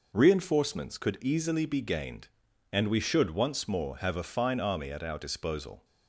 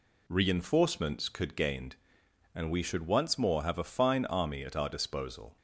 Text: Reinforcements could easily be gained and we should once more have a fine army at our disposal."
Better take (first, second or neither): first